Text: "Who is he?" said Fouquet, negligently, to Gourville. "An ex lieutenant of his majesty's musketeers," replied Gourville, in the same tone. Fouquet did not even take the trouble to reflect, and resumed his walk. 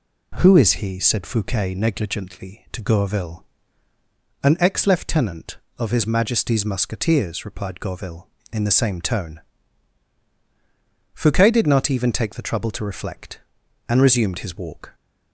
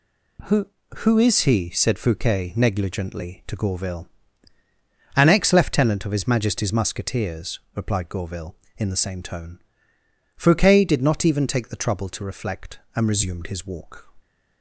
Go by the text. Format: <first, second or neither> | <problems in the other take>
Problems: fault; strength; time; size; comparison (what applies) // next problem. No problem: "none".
first | says "Who" twice; at 0.9 s